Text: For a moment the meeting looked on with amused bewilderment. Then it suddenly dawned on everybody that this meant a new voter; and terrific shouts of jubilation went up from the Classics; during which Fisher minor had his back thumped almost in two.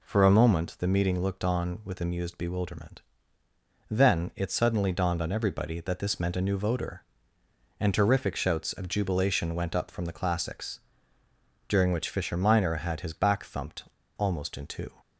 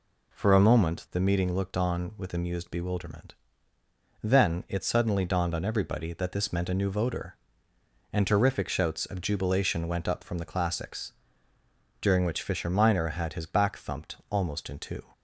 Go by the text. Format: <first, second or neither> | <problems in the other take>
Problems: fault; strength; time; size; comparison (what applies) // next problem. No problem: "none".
second | pauses between "thumped" and "almost"; slight; at 13.8 s; 0.32 s long